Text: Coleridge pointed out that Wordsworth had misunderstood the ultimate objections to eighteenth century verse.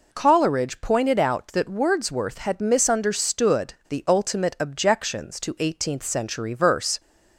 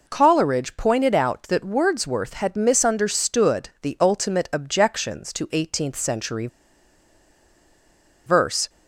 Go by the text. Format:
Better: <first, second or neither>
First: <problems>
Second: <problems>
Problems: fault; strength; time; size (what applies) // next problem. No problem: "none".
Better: first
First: none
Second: pauses between "century" and "verse"; strong; at 6.4 s; 1.7 s long